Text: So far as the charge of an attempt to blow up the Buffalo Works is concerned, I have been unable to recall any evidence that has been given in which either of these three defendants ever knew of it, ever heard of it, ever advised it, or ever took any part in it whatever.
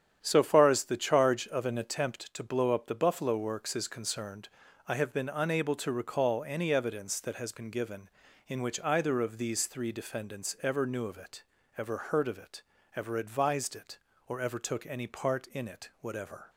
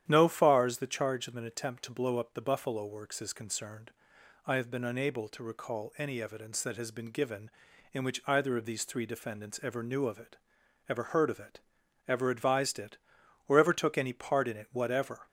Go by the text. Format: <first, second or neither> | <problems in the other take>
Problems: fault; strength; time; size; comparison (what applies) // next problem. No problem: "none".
first | starts louder than the rest; strong; until 1.0 s; 10 dB; strong in the first // says "No" for "So"; at 0.0 s